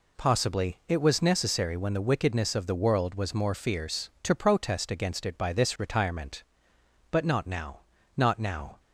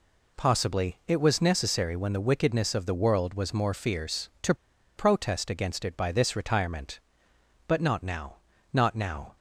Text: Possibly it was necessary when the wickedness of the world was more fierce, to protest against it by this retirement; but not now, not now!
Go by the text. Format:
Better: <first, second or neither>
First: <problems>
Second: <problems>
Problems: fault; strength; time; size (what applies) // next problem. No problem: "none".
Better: first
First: none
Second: pauses between "to" and "protest"; at 4.5 s; 0.42 s long